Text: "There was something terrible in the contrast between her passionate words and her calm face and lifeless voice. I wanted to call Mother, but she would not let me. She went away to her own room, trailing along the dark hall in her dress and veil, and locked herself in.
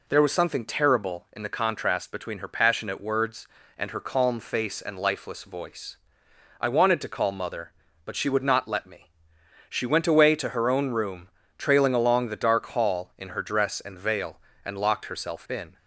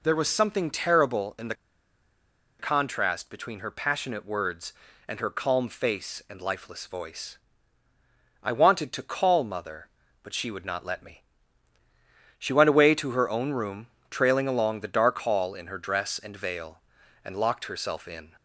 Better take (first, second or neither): first